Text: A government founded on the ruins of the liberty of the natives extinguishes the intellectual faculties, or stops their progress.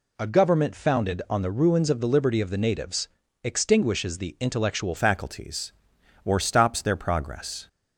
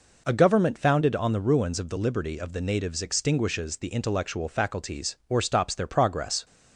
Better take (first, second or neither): second